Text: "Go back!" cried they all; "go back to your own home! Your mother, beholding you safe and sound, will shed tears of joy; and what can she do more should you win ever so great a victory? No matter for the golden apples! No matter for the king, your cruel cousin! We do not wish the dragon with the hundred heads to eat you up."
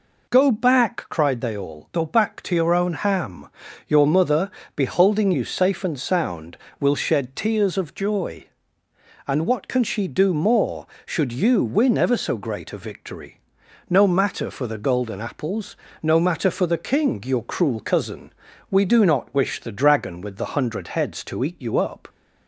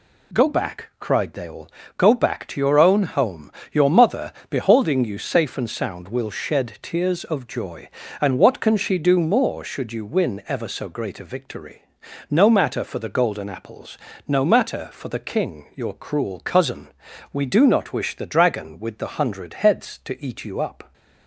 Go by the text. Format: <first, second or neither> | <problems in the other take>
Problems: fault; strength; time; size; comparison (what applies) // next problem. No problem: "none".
second | says "ham" for "home"; at 2.9 s